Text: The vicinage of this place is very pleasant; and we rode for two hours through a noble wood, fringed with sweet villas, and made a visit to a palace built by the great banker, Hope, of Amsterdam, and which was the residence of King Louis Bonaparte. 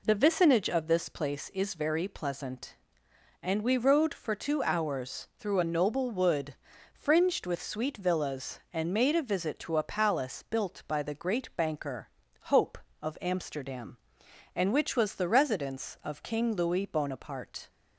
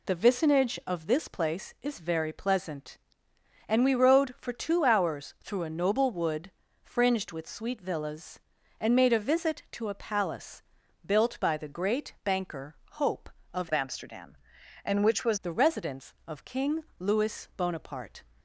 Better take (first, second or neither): first